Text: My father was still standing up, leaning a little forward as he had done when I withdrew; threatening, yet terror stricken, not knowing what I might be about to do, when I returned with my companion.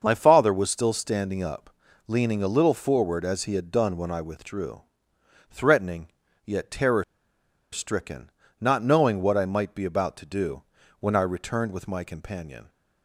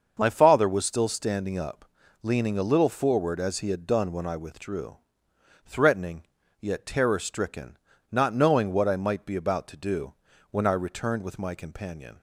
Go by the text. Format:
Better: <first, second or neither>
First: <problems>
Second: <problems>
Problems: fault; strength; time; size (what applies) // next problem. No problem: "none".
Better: second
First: starts louder than the rest; until 1.0 s; 6.5 dB // pauses between "terror" and "stricken"; noticeable; at 7.0 s; 0.69 s long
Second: starts louder than the rest; until 1.1 s; 6.5 dB